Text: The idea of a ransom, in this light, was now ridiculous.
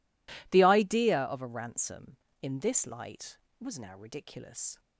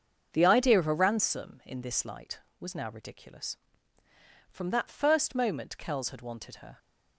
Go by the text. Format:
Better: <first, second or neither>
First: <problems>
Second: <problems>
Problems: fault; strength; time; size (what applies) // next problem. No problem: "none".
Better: first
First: none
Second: starts louder than the rest; until 1.3 s; 7 dB // goes on to say "From that first moment Kells had wanted her"; strong; from 4.5 s on; 2.2 s long